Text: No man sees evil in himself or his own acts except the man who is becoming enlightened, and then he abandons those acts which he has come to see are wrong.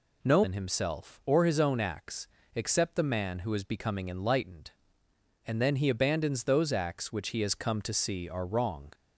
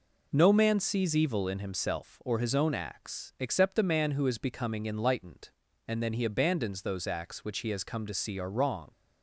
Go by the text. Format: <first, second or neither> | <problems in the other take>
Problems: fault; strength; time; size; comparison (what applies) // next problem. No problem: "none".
second | skips "man sees evil"; at 0.4 s // pauses between "acts" and "except"; slight; at 2.2 s; 0.28 s long